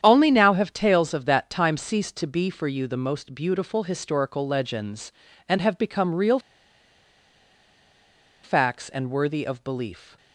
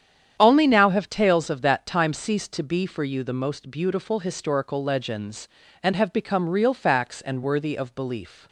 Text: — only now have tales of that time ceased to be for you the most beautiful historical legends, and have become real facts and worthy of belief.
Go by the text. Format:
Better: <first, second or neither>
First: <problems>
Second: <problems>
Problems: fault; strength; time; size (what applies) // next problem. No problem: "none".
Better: second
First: starts louder than the rest; strong; until 1.0 s; 9 dB // pauses between "real" and "facts"; strong; at 6.3 s; 2.0 s long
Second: starts louder than the rest; strong; until 1.4 s; 9 dB